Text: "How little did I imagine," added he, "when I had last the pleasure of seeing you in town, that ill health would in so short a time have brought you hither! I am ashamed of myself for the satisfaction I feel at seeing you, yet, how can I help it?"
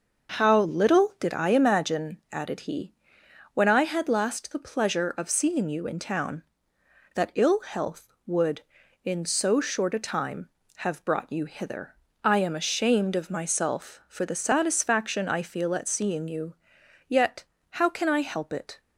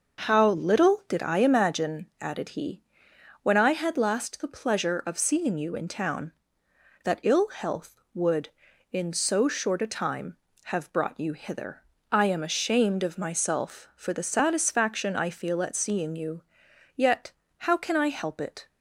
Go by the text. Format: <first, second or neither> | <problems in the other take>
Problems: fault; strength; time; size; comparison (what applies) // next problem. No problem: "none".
neither | none